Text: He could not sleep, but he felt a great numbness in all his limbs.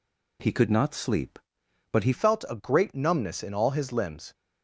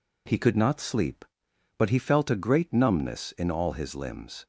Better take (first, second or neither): second